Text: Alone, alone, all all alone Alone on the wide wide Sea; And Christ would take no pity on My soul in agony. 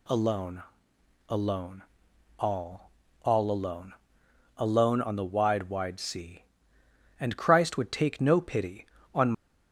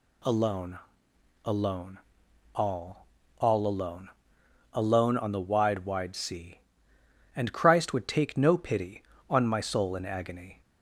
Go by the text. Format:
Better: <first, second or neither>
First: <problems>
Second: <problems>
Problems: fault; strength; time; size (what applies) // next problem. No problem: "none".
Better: second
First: pauses between "all" and "all"; slight; at 2.9 s; 0.34 s long // pauses between "alone" and "Alone"; noticeable; at 3.9 s; 0.64 s long // stops before "My soul in agony"; at 9.3 s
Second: pauses between "all" and "all"; slight; at 3.0 s; 0.34 s long // pauses between "alone" and "Alone"; noticeable; at 4.0 s; 0.64 s long